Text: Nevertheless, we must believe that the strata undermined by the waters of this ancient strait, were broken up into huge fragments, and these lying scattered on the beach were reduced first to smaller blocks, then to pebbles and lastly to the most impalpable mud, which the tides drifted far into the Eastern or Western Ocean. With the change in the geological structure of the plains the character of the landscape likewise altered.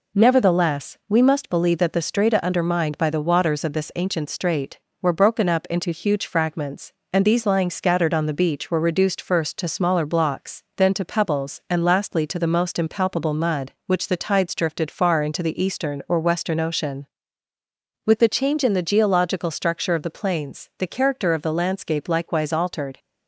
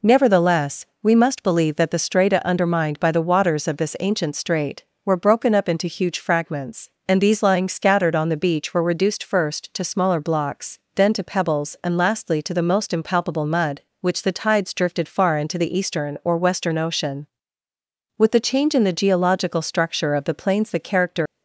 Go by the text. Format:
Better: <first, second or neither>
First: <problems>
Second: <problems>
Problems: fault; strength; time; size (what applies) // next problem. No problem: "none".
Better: first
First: none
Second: stops before "of the landscape likewise altered"; at 21.2 s